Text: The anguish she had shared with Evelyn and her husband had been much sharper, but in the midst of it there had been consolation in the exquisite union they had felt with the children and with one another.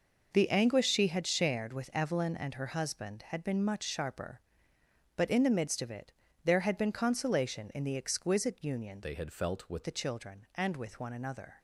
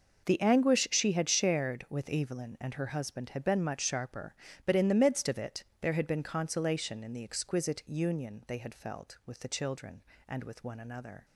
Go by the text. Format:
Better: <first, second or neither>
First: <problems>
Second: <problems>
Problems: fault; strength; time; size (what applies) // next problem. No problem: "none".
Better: second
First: pauses between "it" and "there"; slight; at 6.1 s; 0.34 s long // changes voice from "they" to "with"; from 9.0 to 9.8 s; 0.8 s long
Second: pauses between "it" and "there"; slight; at 5.6 s; 0.16 s long